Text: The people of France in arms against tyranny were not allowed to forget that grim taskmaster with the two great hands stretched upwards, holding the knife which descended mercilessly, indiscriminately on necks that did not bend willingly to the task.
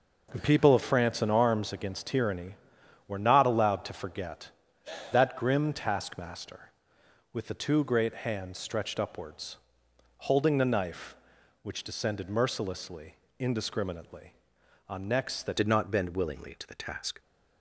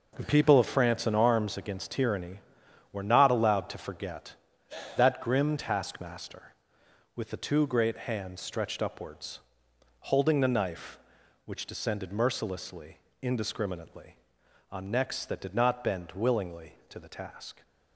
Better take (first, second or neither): second